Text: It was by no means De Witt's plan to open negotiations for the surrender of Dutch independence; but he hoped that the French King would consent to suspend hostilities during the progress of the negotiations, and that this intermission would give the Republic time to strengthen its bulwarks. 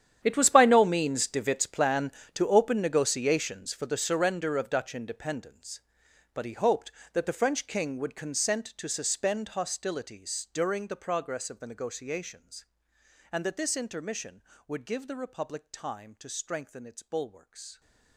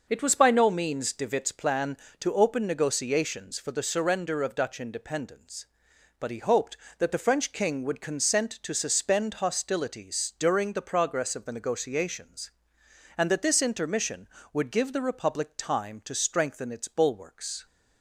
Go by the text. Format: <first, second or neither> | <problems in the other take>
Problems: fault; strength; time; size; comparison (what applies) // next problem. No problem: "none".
second | gets quieter; strong; throughout; 18 dB